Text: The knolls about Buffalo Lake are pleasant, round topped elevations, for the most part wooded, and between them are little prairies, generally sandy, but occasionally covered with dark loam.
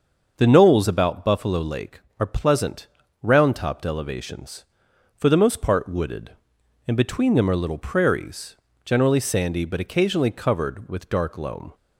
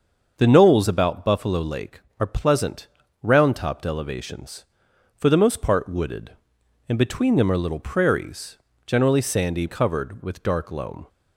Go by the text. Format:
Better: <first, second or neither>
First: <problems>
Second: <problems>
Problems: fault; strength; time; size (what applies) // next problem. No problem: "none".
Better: first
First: starts louder than the rest; until 1.3 s; 6.5 dB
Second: starts louder than the rest; until 1.3 s; 6.5 dB // skips "but occasionally"; at 9.6 s